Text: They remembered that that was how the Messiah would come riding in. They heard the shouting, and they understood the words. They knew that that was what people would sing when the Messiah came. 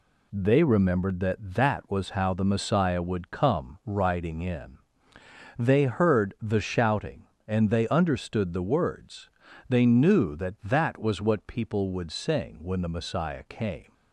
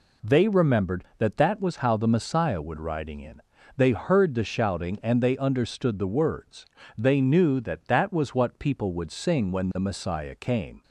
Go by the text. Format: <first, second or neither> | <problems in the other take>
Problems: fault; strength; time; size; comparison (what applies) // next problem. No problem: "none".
first | skips "come"; at 2.7 s